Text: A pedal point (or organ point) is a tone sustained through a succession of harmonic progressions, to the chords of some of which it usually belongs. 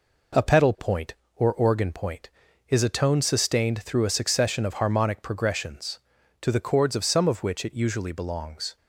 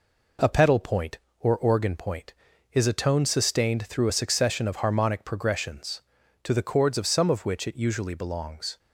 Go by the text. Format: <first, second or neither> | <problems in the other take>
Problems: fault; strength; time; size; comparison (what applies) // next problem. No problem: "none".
neither | none